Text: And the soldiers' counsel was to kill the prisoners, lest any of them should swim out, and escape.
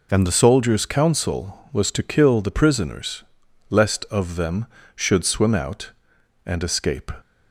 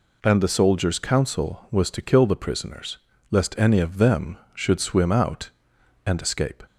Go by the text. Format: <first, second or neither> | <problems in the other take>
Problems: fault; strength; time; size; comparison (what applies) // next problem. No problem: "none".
second | skips "any"; at 4.0 s